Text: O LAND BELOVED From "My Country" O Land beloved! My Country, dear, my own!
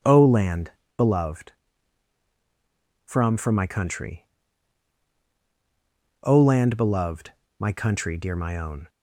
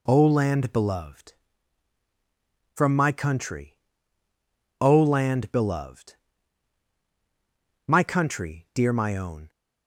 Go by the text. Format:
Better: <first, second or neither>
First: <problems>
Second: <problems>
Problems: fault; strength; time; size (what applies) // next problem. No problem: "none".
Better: second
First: pauses between "LAND" and "BELOVED"; slight; at 0.7 s; 0.26 s long // says "From" twice; at 3.3 s // pauses between "Country" and "O"; strong; at 4.2 s; 1.9 s long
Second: pauses between "Country" and "O"; at 3.7 s; 1.0 s long